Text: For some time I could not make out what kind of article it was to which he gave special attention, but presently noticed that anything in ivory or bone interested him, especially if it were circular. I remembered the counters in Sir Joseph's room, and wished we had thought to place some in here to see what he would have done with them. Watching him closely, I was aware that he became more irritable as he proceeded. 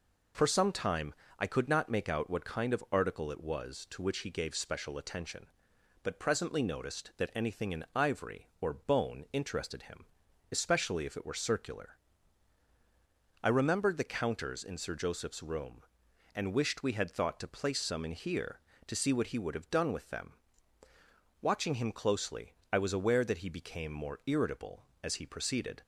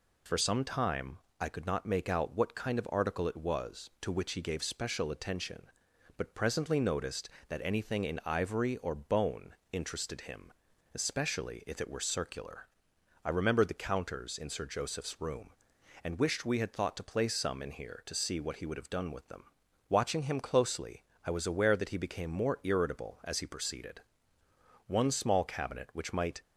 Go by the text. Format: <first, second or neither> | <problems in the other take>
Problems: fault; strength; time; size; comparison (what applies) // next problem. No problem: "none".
first | pauses between "time" and "I"; slight; at 1.1 s; 0.20 s long; slight in the first // pauses between "bone" and "interested"; slight; at 9.5 s; 0.16 s long // goes on to say "One small cabinet which might"; from 24.8 s on; 1.5 s long